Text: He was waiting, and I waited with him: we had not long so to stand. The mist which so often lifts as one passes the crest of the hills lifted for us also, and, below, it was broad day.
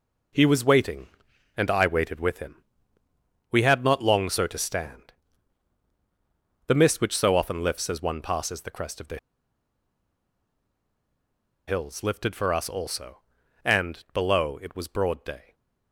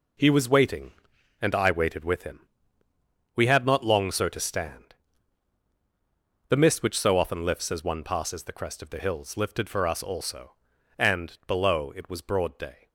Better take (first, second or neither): second